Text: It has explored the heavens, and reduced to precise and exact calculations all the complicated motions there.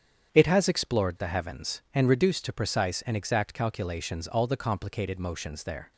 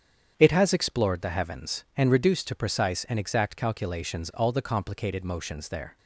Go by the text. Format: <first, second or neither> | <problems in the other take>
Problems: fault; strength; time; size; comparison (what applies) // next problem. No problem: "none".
neither | starts louder than the rest; strong; the same in both